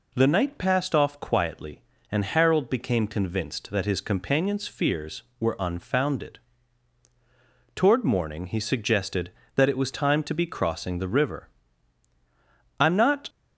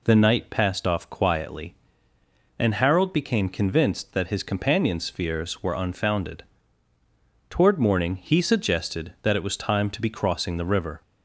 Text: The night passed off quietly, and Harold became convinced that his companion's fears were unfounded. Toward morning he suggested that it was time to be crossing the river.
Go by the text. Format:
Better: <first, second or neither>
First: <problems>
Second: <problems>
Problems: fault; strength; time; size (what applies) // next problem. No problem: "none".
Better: second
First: goes on to say "I'm not"; slight; from 12.8 s on; 0.48 s long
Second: none